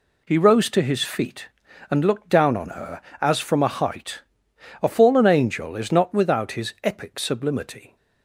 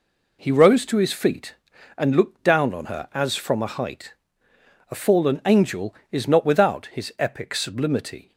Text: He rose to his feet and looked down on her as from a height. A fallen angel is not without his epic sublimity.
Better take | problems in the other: neither | none

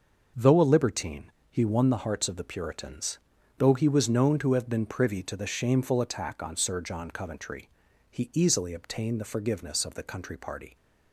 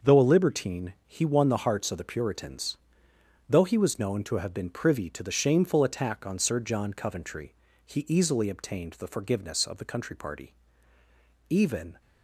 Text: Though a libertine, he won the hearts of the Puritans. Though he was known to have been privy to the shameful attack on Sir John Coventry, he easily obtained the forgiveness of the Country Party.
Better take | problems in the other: first | starts louder than the rest; until 1.1 s; 6 dB // goes on to say "Even"; from 11.4 s on; 0.52 s long

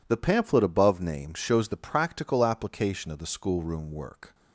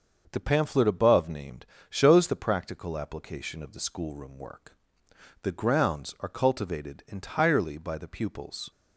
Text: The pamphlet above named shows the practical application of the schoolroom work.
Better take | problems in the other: first | starts louder than the rest; until 1.3 s; 6.5 dB // pauses between "named" and "shows"; slight; at 1.6 s; 0.22 s long // goes on to say "The grounds are cultivated entirely by the pupils"; strong; from 5.4 s on; 3.2 s long

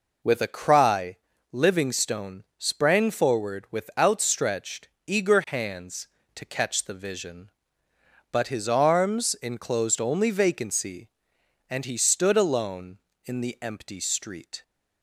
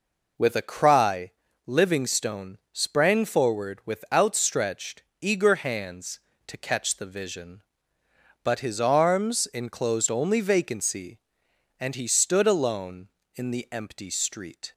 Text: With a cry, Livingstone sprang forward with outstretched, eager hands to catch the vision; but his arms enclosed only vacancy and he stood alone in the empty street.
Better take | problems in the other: neither | pauses between "Livingstone" and "sprang"; slight; the same in both

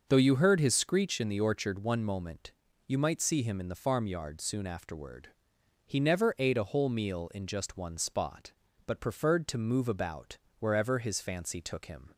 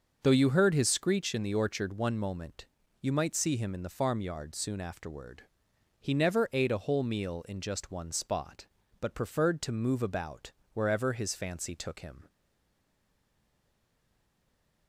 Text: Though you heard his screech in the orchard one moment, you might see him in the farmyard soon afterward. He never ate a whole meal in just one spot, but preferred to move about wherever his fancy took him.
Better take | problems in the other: first | pauses between "about" and "wherever"; slight; at 10.5 s; 0.22 s long; slight in the first // stays silent after the last word; strong; from 12.2 s on; 2.6 s long

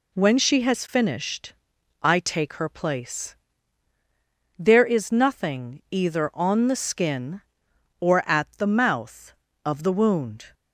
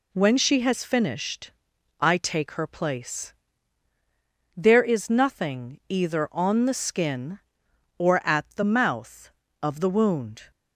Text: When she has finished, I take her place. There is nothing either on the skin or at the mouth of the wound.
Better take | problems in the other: neither | none

